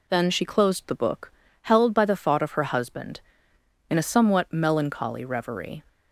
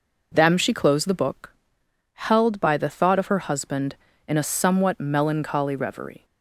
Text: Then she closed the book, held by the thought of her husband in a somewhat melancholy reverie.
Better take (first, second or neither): first